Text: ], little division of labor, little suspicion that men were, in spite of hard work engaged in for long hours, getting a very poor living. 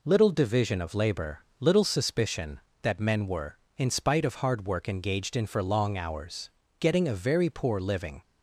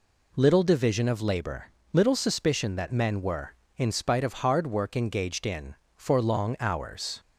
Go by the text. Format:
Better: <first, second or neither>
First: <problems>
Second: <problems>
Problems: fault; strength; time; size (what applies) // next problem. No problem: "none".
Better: first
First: none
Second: stops before "getting a very poor living"; at 7.1 s